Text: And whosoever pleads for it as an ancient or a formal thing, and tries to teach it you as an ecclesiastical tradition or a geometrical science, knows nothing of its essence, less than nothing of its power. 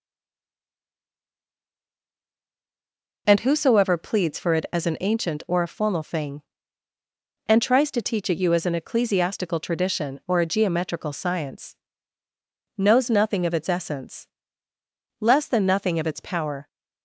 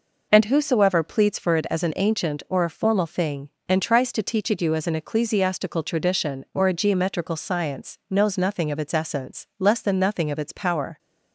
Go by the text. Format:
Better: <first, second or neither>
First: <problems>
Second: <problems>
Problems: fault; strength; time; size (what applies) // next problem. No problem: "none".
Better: second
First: stays silent before the first word; strong; until 3.2 s; 3.2 s long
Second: none